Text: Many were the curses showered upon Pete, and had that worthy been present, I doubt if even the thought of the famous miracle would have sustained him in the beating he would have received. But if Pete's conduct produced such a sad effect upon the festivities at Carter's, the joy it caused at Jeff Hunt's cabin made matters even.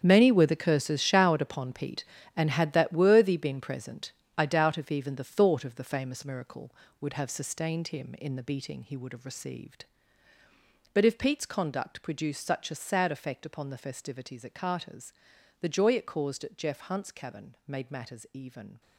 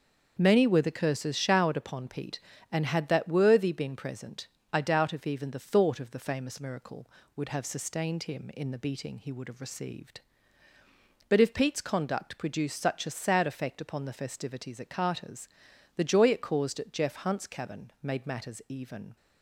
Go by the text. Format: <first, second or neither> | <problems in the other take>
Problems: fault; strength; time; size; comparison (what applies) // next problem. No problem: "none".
second | gets quieter; strong; throughout; 13 dB // starts louder than the rest; strong; until 1.0 s; 8 dB; also in the second